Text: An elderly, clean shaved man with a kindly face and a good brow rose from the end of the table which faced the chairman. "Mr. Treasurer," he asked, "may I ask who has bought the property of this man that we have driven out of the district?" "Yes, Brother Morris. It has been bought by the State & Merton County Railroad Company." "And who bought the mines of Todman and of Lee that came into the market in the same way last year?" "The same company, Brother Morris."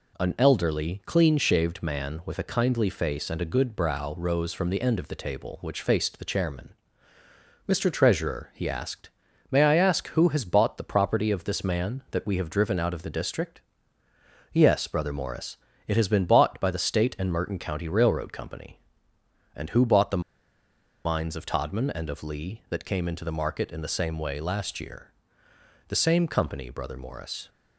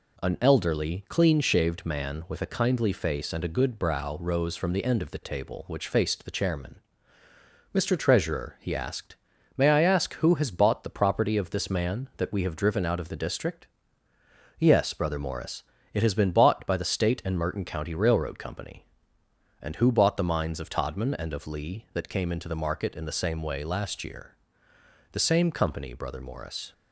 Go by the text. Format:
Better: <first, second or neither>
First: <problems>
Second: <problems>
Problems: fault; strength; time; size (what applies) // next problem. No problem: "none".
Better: second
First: pauses between "the" and "mines"; noticeable; at 20.2 s; 0.82 s long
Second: none